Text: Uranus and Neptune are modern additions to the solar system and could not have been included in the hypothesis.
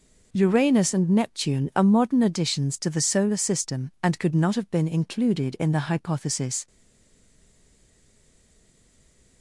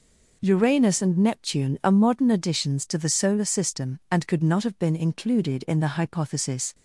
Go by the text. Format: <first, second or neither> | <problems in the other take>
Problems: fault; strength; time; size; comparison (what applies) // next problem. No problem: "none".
second | stays silent after the last word; strong; from 6.6 s on; 2.8 s long